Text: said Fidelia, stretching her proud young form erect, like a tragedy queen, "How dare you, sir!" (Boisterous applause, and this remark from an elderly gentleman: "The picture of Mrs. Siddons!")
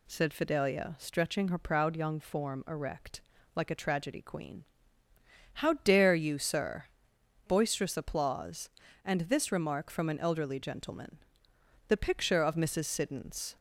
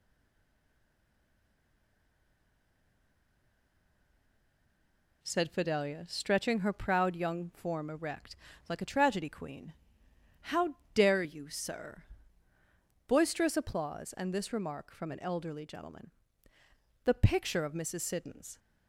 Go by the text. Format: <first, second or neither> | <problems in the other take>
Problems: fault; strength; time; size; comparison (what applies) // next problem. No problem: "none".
first | stays silent before the first word; strong; until 5.2 s; 5.2 s long // pauses between "How" and "dare"; slight; at 10.7 s; 0.18 s long